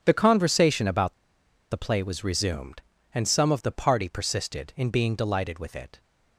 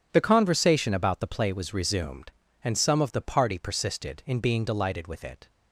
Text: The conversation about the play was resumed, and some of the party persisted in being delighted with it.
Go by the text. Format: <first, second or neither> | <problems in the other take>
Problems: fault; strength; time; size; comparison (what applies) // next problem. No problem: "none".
second | starts louder than the rest; strong; until 1.0 s; 9.5 dB // pauses between "about" and "the"; noticeable; at 1.1 s; 0.56 s long